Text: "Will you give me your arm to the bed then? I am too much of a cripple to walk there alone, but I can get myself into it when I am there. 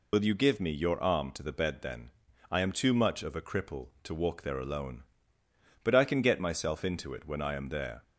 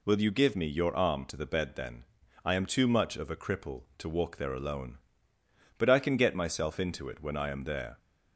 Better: second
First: loses the start of "Will"; at 0.1 s; 50 ms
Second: none

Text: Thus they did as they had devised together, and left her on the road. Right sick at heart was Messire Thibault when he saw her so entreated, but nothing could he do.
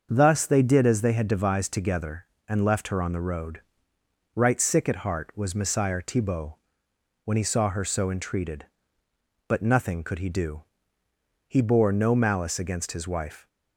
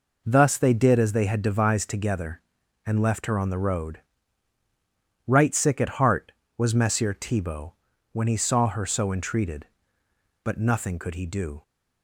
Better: second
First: starts louder than the rest; until 1.1 s; 6.5 dB // pauses between "Thibault" and "when"; noticeable; at 6.5 s; 0.66 s long // goes on to say "He bore no malice against his wife"; strong; from 11.4 s on; 2.0 s long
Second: pauses between "Thibault" and "when"; at 7.7 s; 0.38 s long

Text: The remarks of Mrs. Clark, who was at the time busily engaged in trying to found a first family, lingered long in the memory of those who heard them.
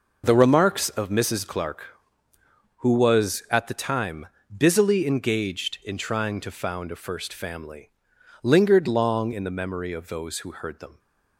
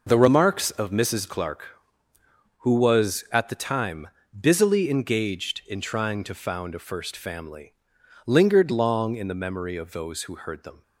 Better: neither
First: pauses between "time" and "busily"; slight; at 4.2 s; 0.32 s long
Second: pauses between "time" and "busily"; slight; at 4.0 s; 0.34 s long

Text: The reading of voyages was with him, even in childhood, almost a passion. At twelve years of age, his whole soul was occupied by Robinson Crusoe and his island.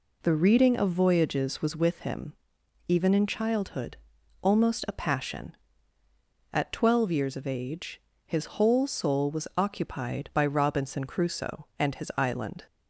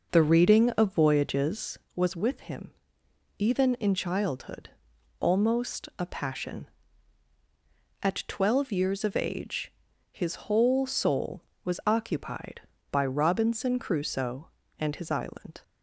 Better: first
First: none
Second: starts louder than the rest; noticeable; until 1.9 s; 5.5 dB

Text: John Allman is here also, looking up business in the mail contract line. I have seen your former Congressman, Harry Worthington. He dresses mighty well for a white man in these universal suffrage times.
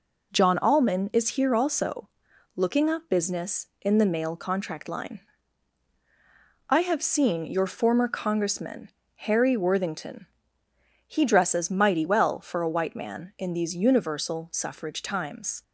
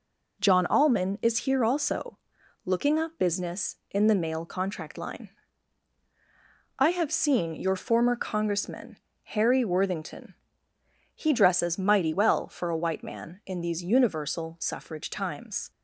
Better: neither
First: none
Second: none

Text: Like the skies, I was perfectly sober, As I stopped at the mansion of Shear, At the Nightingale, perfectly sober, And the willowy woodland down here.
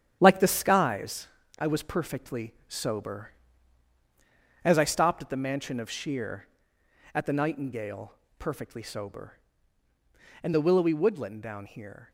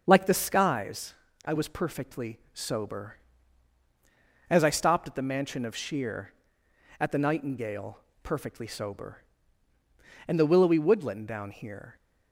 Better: second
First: gets quieter; strong; throughout; 8 dB // starts louder than the rest; strong; until 1.2 s; 9 dB // pauses between "perfectly" and "sober"; slight; at 2.5 s; 0.16 s long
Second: starts louder than the rest; until 1.0 s; 7 dB // pauses between "perfectly" and "sober"; slight; at 2.3 s; 0.16 s long

